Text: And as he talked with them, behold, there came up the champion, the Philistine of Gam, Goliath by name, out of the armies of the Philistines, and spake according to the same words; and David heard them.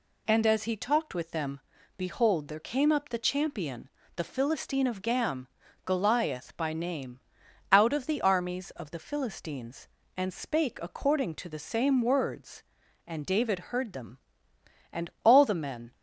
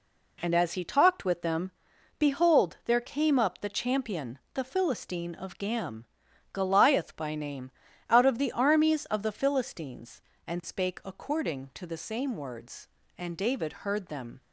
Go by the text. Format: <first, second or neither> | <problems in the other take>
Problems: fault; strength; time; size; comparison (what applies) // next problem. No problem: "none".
second | goes on to say "And all the men"; noticeable; from 14.9 s on; 1.0 s long